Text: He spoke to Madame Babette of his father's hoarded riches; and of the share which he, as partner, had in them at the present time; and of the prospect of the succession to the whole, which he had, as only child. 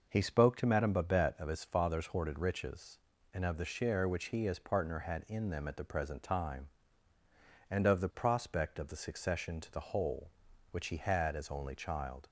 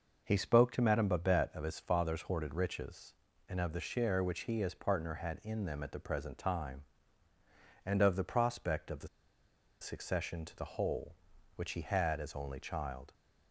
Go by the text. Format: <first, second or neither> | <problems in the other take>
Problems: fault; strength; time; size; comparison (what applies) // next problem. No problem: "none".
first | pauses between "the" and "succession"; noticeable; at 9.0 s; 0.73 s long